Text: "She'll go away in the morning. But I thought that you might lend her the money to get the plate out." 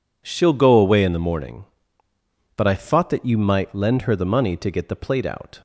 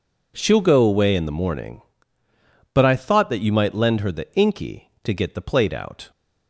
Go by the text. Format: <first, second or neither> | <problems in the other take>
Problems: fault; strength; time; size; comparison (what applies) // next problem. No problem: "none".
first | says "inky" for "money"; at 4.3 s